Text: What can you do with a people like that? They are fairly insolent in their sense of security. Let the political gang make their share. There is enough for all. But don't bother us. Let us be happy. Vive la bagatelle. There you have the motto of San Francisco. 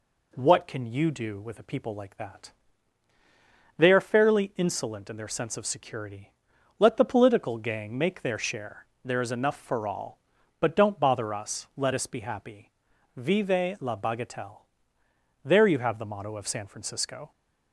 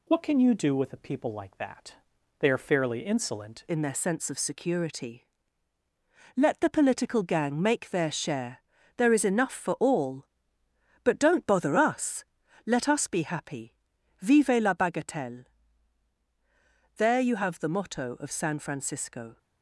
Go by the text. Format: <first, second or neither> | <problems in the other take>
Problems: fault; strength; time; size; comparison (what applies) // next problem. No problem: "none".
first | changes voice at "in"; from 3.6 s on; 15.7 s long